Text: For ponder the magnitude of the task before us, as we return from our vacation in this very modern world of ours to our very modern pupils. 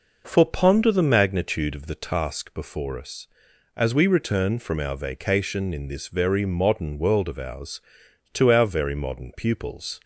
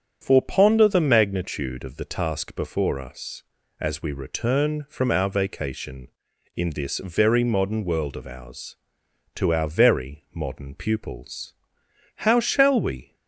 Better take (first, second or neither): first